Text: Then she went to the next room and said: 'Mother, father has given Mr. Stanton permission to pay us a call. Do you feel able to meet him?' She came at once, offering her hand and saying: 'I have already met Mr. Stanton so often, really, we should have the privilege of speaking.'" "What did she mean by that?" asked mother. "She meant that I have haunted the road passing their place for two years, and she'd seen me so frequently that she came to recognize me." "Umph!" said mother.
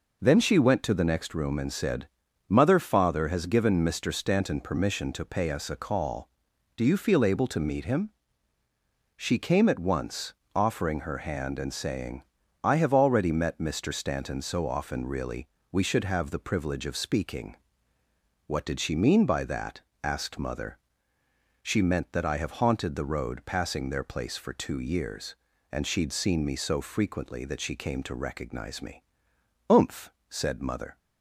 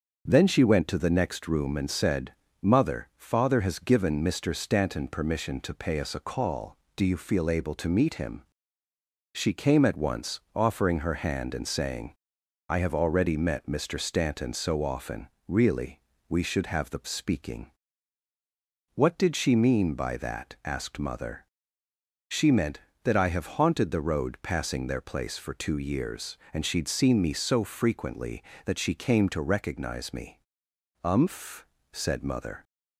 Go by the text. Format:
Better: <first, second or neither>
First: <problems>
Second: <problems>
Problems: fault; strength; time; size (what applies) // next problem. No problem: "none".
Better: first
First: none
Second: starts louder than the rest; until 1.2 s; 6.5 dB // skips "privilege of"; at 17.0 s